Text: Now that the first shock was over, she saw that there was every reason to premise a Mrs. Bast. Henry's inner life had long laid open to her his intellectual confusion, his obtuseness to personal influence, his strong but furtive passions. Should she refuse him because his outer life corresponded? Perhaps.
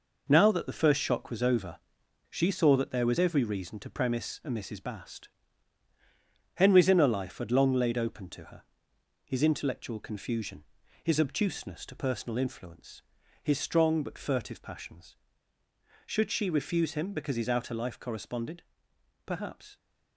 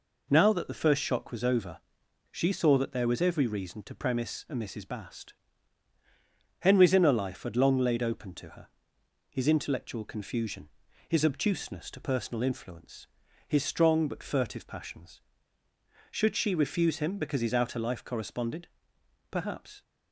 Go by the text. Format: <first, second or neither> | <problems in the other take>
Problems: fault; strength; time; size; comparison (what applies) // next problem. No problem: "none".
second | gets quieter; strong; throughout; 7.5 dB // pauses between "her" and "his"; noticeable; at 8.6 s; 0.62 s long; noticeable in the second